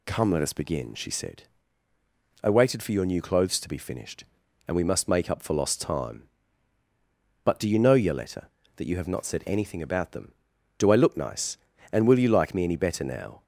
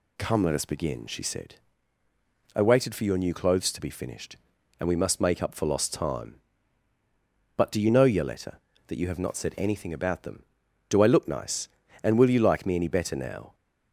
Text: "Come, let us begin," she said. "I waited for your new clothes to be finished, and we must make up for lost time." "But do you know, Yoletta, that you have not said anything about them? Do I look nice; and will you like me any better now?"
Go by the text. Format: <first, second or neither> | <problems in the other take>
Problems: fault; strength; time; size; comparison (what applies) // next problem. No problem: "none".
neither | none